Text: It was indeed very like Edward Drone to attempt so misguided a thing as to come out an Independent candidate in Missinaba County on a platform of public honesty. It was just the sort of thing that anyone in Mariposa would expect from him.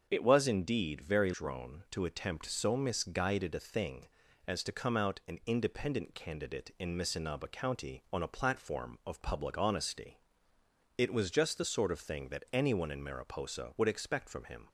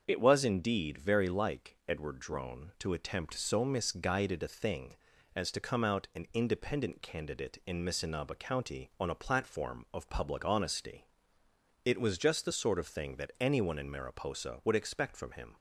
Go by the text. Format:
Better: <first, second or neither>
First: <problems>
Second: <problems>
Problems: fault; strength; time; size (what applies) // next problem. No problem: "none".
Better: second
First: starts louder than the rest; until 1.1 s; 6.5 dB // skips "like Edward"; at 1.3 s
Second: starts louder than the rest; until 1.0 s; 6.5 dB